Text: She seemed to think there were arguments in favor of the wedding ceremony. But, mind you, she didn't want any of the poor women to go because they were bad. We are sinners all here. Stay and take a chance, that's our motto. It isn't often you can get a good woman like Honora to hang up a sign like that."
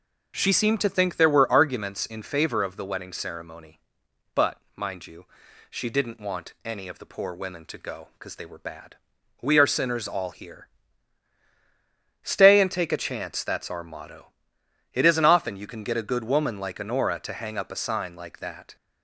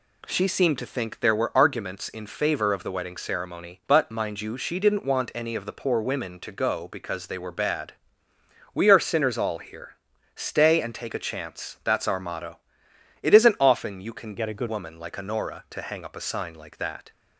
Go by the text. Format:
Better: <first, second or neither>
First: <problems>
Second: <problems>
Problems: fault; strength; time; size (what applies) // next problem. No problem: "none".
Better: first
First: none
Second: changes voice from "get" to "good"; from 14.3 to 14.6 s; 0.3 s long